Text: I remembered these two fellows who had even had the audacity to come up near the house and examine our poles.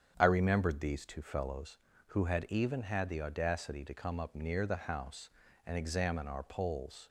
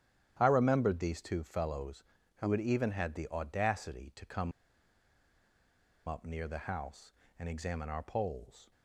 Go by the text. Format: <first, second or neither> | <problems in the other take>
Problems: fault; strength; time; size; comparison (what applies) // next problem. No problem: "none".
first | starts louder than the rest; strong; until 1.4 s; 10.5 dB; strong in the first // pauses between "come" and "up"; strong; at 4.5 s; 1.5 s long